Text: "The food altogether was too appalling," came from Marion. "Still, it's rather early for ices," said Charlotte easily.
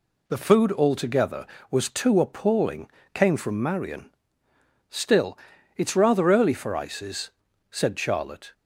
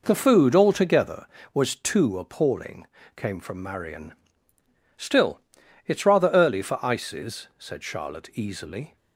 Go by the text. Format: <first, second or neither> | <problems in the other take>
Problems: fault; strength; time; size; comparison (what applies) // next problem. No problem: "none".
second | stops before "easily"; at 8.5 s